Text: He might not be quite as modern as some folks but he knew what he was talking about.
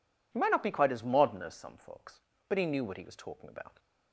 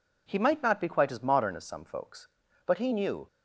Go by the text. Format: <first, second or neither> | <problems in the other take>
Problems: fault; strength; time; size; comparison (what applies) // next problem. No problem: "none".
first | stops before "what he was talking about"; at 3.2 s